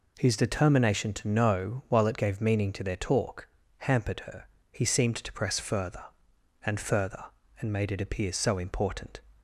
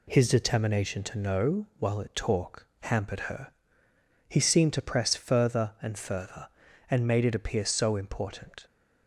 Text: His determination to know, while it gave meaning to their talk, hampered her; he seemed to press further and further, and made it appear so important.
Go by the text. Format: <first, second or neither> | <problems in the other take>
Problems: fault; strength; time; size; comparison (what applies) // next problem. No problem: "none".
first | skips "gave meaning to their"; at 2.1 s